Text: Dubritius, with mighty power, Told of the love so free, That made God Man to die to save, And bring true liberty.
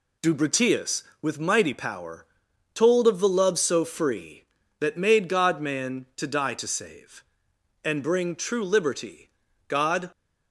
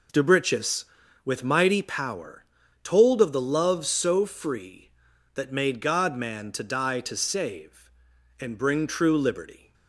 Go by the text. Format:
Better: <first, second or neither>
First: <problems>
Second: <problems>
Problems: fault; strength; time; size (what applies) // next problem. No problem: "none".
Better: second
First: goes on to say "God"; slight; from 9.6 s on; 0.40 s long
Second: none